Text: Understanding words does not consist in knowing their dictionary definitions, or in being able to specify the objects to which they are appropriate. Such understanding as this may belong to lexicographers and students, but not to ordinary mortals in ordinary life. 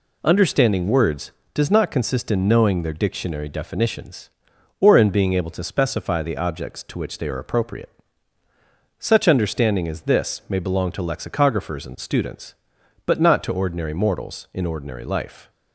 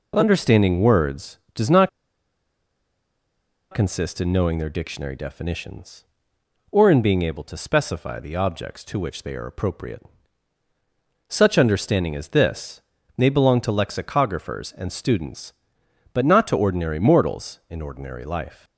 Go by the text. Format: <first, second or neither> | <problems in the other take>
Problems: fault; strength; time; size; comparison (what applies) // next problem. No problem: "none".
first | pauses between "not" and "consist"; strong; at 1.8 s; 1.8 s long // pauses between "this" and "may"; slight; at 12.8 s; 0.34 s long